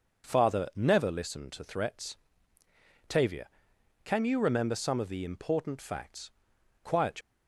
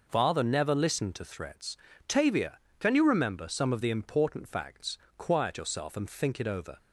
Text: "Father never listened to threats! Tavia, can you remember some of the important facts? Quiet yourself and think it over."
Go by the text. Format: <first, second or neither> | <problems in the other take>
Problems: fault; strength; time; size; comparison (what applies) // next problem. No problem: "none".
second | stops before "yourself and think it over"; at 7.2 s